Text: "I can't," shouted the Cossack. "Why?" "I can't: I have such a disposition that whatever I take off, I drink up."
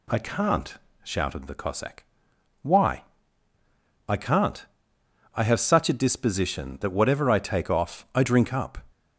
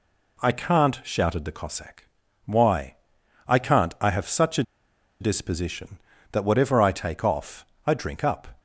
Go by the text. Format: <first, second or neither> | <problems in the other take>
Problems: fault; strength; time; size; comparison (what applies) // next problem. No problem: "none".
first | pauses between "a" and "disposition"; noticeable; at 4.6 s; 0.56 s long